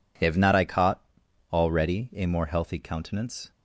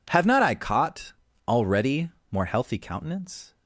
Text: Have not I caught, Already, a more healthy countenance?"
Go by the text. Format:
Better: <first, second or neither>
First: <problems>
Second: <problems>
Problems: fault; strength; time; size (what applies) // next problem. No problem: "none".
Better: first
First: none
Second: skips "a"; at 2.1 s